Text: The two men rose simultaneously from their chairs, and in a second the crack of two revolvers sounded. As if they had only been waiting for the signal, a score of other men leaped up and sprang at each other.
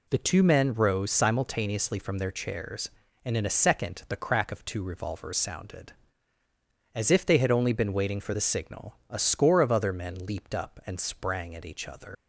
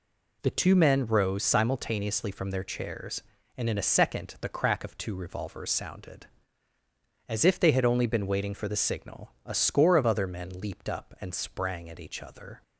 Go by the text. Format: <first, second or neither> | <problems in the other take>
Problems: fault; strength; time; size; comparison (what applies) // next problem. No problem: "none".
second | leaves "other" unfinished; at 12.1 s; 130 ms